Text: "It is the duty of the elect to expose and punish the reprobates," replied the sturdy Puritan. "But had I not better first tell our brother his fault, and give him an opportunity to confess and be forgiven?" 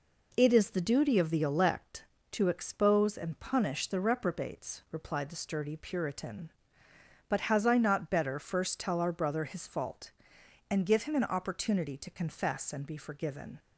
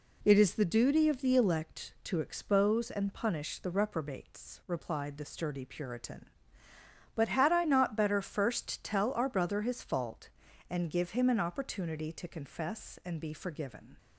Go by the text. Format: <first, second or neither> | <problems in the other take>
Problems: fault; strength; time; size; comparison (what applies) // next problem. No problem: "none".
second | says "has" for "had"; at 7.5 s